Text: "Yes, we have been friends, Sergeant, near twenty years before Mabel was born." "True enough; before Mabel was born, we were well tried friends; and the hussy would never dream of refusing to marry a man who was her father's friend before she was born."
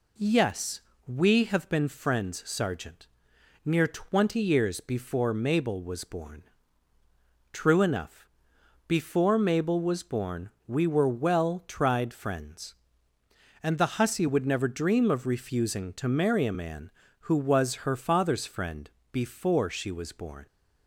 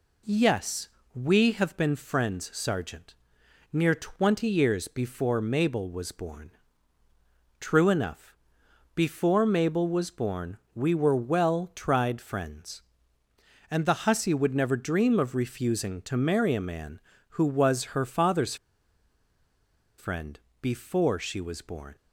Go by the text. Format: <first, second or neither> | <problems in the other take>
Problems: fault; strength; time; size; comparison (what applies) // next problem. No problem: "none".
first | pauses between "father's" and "friend"; strong; at 18.5 s; 1.4 s long // pauses between "friend" and "before"; slight; at 20.4 s; 0.20 s long; slight in the first